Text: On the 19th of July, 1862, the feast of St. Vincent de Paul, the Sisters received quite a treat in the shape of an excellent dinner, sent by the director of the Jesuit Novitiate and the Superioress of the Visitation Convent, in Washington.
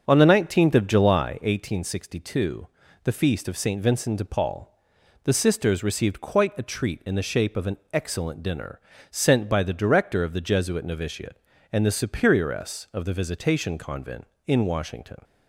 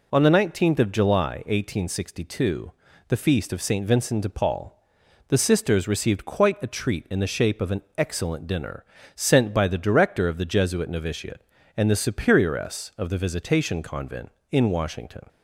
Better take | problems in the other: second | starts louder than the rest; until 1.7 s; 7 dB // pauses between "an" and "excellent"; slight; at 7.7 s; 0.16 s long; slight in the second

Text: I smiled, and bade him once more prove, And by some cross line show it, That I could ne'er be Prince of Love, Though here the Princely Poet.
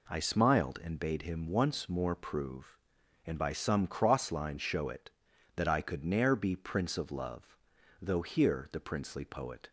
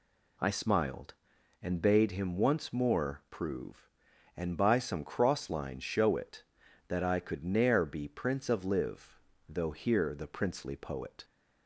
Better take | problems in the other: first | says "Live" for "Love"; at 8.6 s

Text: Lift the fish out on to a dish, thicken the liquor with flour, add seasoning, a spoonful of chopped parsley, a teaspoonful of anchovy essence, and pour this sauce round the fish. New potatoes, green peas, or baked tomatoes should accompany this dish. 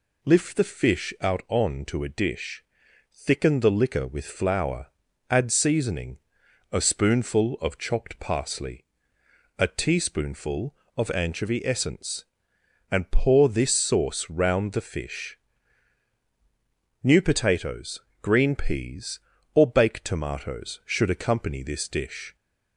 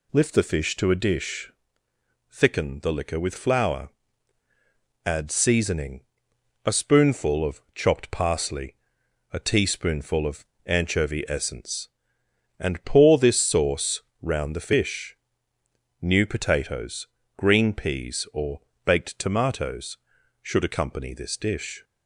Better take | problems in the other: first | skips "out on"; at 0.7 s // pauses between "of" and "anchovy"; slight; at 10.4 s; 0.20 s long // pauses between "sauce" and "round"; slight; at 14.0 s; 0.18 s long // pauses between "or" and "baked"; slight; at 18.6 s; 0.24 s long

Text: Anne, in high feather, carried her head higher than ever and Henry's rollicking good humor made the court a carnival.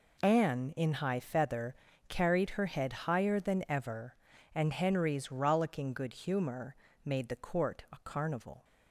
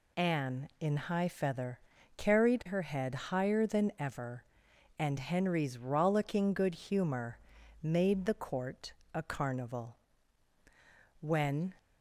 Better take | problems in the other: first | pauses between "humor" and "made"; noticeable; at 7.3 s; 0.46 s long; slight in the first // pauses between "court" and "a"; slight; at 8.9 s; 0.20 s long // goes on to say "When"; from 11.1 s on; 0.56 s long

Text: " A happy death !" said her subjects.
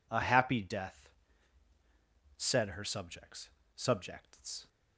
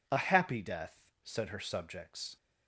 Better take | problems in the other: second | says "subjects" twice; at 3.7 s

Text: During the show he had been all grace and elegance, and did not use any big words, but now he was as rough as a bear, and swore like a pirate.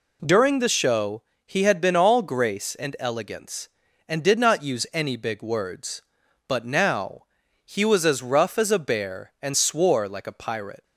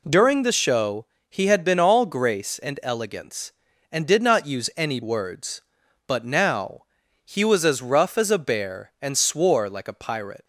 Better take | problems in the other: first | pauses between "show" and "he"; slight; at 1.0 s; 0.24 s long; slight in the first // skips "big"; at 5.0 s // pauses between "now" and "he"; at 6.8 s; 0.42 s long; also in the first

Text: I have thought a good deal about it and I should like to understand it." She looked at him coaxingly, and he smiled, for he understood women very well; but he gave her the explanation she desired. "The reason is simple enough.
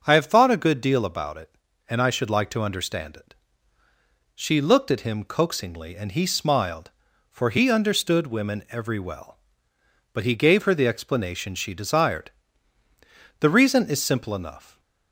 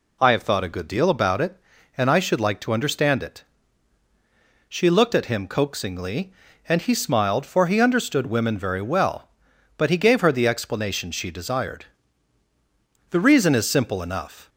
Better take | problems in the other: second | starts louder than the rest; noticeable; until 1.0 s; 6 dB // says "every" for "very"; at 8.7 s

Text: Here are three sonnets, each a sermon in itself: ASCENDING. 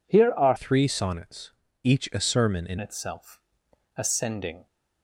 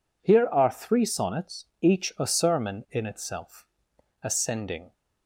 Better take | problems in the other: second | changes voice from "three" to "in"; from 0.5 to 2.7 s; 2.2 s long

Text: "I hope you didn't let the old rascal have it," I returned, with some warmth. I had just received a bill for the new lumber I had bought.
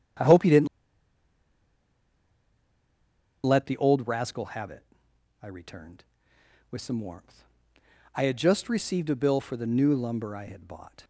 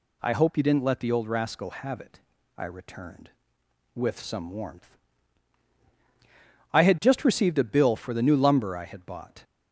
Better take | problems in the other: second | starts louder than the rest; strong; until 3.9 s; 8.5 dB // pauses between "didn't" and "let"; strong; at 0.6 s; 2.7 s long

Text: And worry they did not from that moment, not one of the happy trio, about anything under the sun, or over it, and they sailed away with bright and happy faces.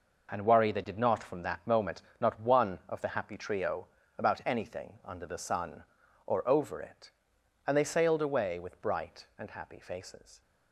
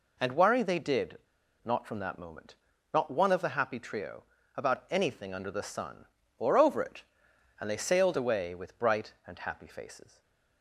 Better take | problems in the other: first | pauses between "did" and "not"; noticeable; at 1.1 s; 0.46 s long // stays silent after the last word; slight; from 10.0 s on; 0.6 s long

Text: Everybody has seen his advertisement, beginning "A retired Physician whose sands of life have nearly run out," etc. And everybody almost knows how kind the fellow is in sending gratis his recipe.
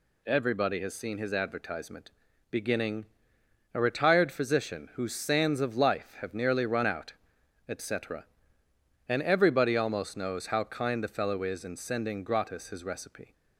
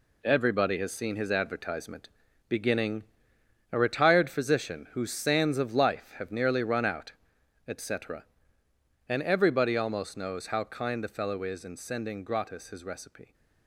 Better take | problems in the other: first | gets quieter; strong; throughout; 8.5 dB // pauses between "beginning" and "A"; noticeable; at 3.0 s; 0.70 s long; noticeable in the first

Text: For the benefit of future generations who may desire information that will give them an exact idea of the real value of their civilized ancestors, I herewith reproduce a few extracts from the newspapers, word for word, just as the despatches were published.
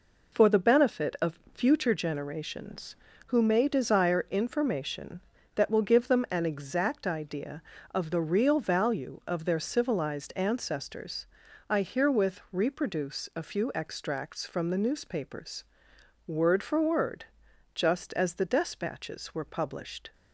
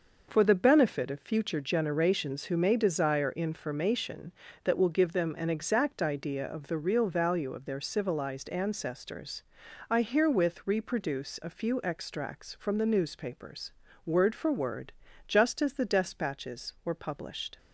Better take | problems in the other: neither | none

